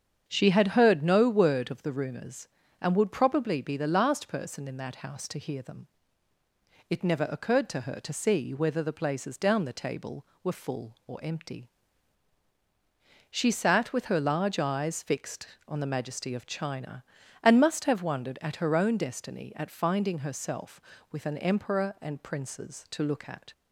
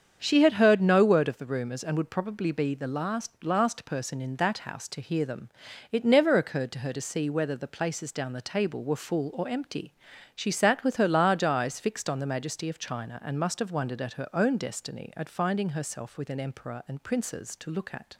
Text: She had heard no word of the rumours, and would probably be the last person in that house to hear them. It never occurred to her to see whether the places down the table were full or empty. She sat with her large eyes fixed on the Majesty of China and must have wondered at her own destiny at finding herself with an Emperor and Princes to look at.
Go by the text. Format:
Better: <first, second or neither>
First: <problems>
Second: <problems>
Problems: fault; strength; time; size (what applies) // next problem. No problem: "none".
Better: first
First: starts louder than the rest; strong; until 1.2 s; 7.5 dB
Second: starts louder than the rest; strong; until 1.2 s; 7.5 dB // says "last" twice; at 3.4 s